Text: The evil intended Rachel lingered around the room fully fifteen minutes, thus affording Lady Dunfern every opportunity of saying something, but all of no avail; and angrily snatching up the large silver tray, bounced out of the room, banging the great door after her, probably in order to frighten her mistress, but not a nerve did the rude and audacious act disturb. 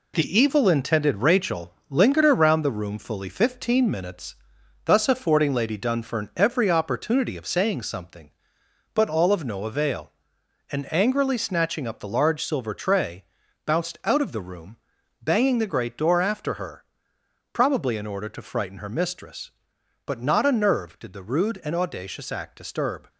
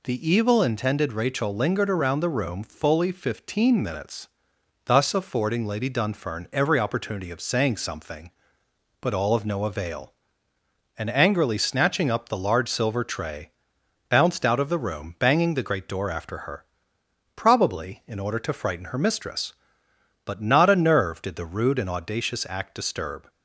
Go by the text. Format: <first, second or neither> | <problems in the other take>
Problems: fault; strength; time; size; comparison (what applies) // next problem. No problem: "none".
second | gets quieter; noticeable; throughout; 6 dB // pauses between "Rachel" and "lingered"; slight; at 1.7 s; 0.16 s long